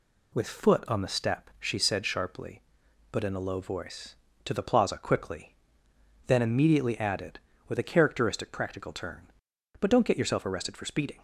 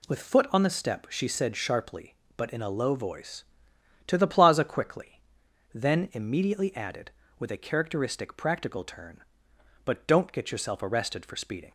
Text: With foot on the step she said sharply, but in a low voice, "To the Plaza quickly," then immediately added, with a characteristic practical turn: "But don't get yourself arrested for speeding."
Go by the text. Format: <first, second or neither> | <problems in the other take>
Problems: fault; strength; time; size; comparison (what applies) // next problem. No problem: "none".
neither | none